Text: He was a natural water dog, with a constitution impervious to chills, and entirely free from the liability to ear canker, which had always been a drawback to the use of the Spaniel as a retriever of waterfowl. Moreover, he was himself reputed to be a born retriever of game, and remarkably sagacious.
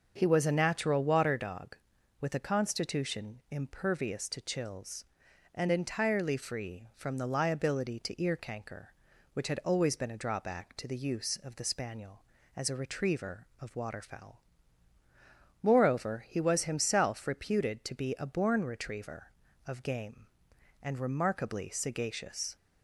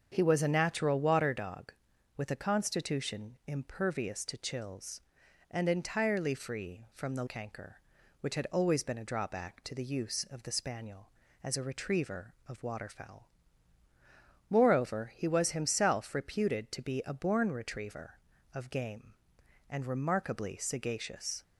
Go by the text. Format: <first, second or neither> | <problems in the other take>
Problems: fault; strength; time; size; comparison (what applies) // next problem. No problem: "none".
first | starts louder than the rest; until 1.1 s; 7 dB; also in the first // skips "liability to ear"; at 7.2 s